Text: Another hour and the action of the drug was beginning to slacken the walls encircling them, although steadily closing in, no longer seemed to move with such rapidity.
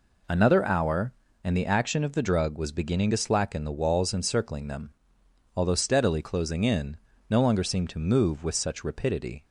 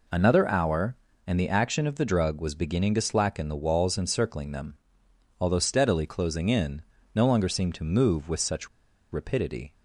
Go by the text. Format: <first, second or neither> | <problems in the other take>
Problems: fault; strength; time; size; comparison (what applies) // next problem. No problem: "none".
first | pauses between "such" and "rapidity"; at 8.6 s; 0.44 s long